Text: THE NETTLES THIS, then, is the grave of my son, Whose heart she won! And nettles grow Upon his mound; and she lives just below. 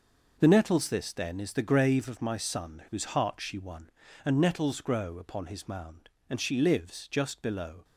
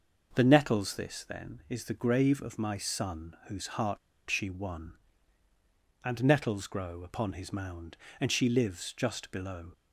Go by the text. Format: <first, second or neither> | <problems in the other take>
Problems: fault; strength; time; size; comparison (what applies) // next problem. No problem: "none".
first | pauses between "heart" and "she"; slight; at 3.9 s; 0.31 s long